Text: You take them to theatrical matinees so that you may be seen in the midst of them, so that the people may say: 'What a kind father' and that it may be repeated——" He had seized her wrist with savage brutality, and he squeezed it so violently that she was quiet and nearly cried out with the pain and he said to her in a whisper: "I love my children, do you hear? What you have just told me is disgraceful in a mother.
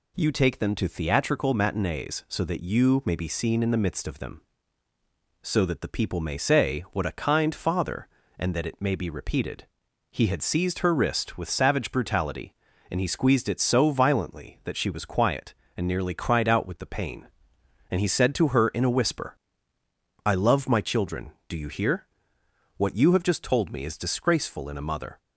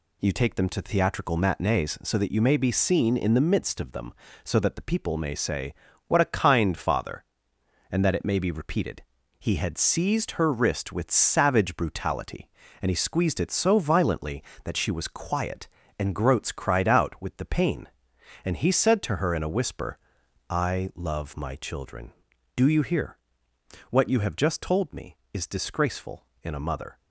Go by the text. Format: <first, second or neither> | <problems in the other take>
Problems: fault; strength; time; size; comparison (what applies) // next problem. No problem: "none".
first | says "groats" for "nearly"; at 16.1 s